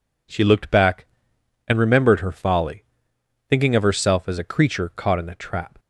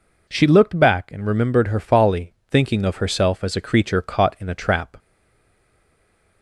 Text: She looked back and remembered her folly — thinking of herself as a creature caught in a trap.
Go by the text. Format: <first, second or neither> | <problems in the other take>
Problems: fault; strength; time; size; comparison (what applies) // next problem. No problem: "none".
first | stays silent after the last word; noticeable; from 4.9 s on; 1.5 s long